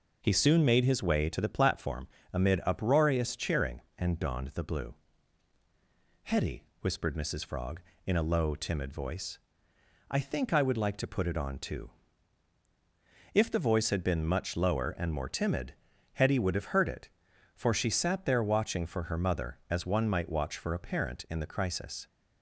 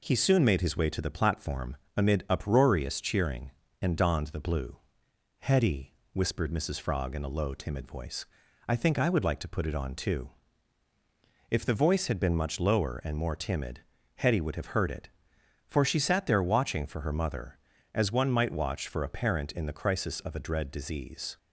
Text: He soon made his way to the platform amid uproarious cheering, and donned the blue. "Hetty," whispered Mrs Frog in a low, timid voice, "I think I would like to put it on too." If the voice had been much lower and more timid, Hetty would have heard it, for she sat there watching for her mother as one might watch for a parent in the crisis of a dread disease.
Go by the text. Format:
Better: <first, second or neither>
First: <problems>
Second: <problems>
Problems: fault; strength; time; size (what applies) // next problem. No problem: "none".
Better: second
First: pauses between "platform" and "amid"; slight; at 2.0 s; 0.26 s long // stops before "of a dread disease"; at 22.0 s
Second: pauses between "platform" and "amid"; slight; at 1.7 s; 0.18 s long